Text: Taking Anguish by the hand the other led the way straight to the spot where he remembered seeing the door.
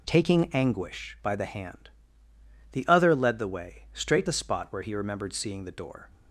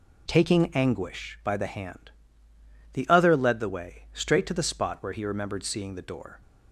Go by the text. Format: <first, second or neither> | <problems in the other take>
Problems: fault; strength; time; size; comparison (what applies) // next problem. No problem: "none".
second | pauses between "hand" and "the"; noticeable; at 1.8 s; 0.84 s long; noticeable in the second // skips "to"; at 4.2 s